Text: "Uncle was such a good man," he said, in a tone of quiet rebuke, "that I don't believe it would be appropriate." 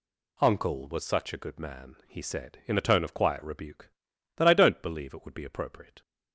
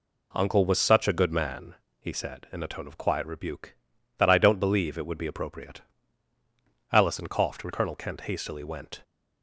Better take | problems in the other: first | goes on to say "Allison coughed and Colonel Kent hastily went"; strong; from 6.9 s on; 2.1 s long

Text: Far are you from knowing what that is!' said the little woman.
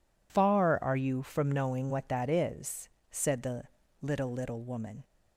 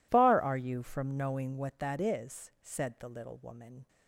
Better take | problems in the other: second | pauses between "the" and "little"; at 3.6 s; 0.38 s long // says "little" twice; at 4.2 s

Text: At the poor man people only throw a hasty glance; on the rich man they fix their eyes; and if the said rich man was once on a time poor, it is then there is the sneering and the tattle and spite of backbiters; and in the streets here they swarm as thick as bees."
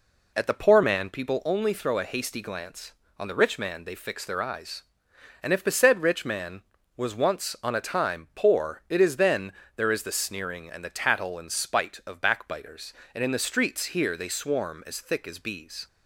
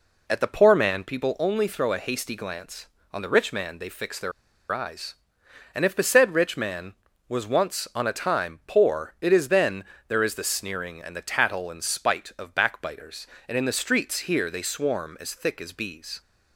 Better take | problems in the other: first | pauses between "their" and "eyes"; at 4.3 s; 0.40 s long // pauses between "then" and "there"; slight; at 9.8 s; 0.24 s long; slight in the first

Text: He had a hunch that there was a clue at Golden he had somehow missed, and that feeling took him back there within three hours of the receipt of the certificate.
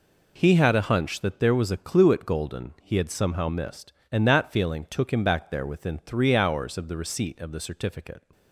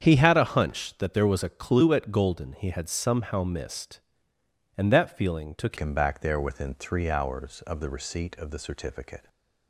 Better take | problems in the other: first | starts louder than the rest; strong; until 1.0 s; 7.5 dB // changes voice at "him"; from 5.7 s on; 3.5 s long // stays silent after the last word; slight; from 9.1 s on; 0.5 s long

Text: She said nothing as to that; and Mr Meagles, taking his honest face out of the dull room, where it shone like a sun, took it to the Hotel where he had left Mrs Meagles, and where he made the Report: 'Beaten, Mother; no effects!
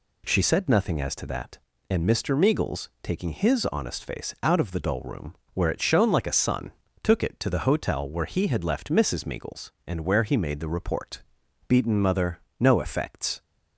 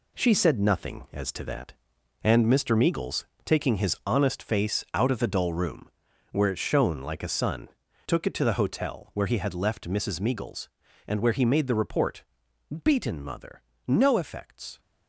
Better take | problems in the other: first | gets quieter; strong; throughout; 7.5 dB

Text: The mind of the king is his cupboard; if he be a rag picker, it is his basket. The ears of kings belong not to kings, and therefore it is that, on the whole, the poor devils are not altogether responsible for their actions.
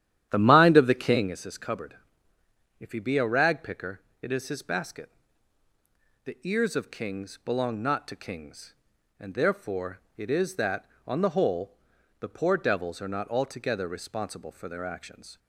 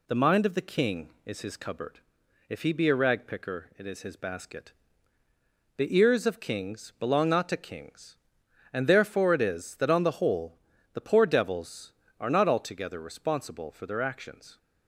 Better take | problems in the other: second | starts louder than the rest; strong; until 1.4 s; 11 dB // pauses between "therefore" and "it"; slight; at 10.0 s; 0.18 s long

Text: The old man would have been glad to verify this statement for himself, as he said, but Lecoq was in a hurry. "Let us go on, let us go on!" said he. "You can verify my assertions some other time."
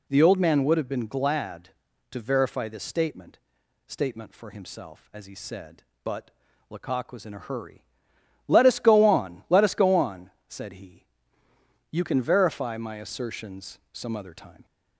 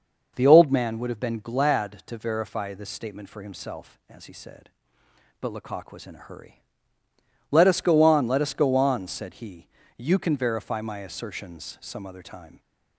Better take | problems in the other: second | says "statement" twice; at 3.8 s // pauses between "but" and "Lecoq"; at 6.3 s; 0.40 s long // pauses between "assertions" and "some"; slight; at 13.7 s; 0.16 s long

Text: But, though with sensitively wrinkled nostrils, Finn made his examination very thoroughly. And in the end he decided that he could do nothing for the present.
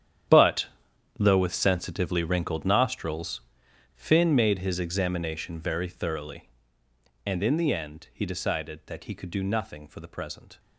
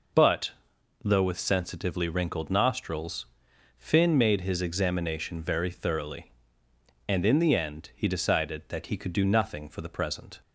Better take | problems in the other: second | gets quieter; strong; throughout; 15.5 dB

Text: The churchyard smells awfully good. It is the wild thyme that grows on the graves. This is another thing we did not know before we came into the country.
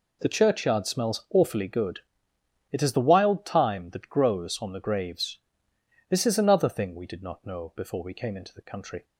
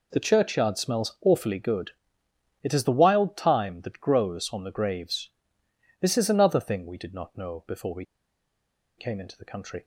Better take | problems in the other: first | pauses between "we" and "came"; noticeable; at 8.0 s; 0.93 s long

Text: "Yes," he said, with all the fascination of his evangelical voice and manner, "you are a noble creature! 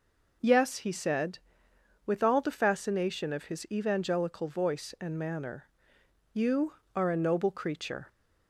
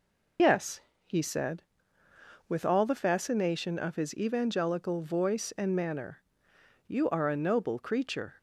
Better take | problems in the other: first | loses the start of "Yes"; at 0.3 s; 80 ms

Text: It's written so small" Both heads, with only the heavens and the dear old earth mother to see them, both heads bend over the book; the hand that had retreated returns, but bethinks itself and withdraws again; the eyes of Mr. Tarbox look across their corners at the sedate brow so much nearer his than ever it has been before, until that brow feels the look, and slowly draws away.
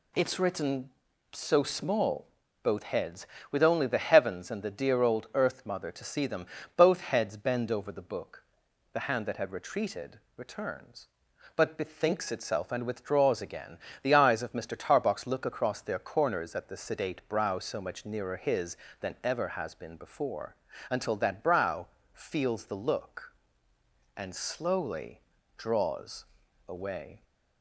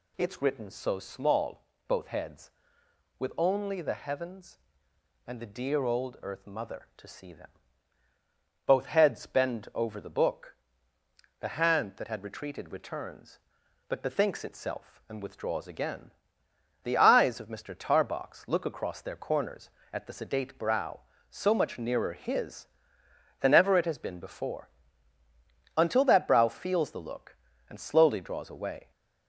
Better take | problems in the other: second | pauses between "small" and "Both"; slight; at 2.2 s; 0.34 s long; slight in the second // pauses between "retreated" and "returns"; slight; at 10.1 s; 0.18 s long // skips "it"; at 19.4 s // pauses between "brow" and "feels"; slight; at 21.8 s; 0.26 s long // pauses between "slowly" and "draws"; slight; at 25.2 s; 0.36 s long // pauses between "draws" and "away"; at 26.2 s; 0.44 s long

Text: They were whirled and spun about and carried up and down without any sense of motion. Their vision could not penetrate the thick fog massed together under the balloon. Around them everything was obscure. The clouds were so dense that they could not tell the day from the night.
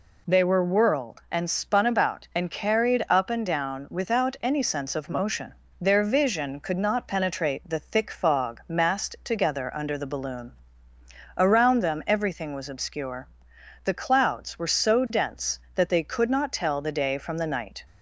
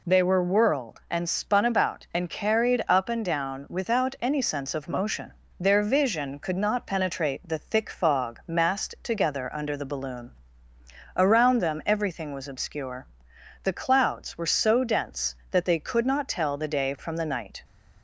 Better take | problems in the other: neither | none

